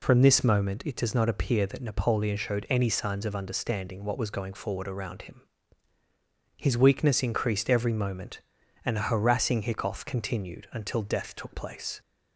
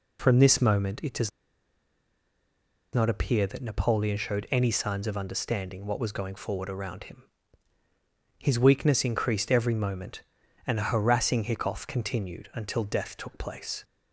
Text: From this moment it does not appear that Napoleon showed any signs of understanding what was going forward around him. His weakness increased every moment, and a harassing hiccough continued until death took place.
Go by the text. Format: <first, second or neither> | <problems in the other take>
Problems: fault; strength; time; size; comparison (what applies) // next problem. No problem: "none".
first | pauses between "does" and "not"; strong; at 1.3 s; 1.6 s long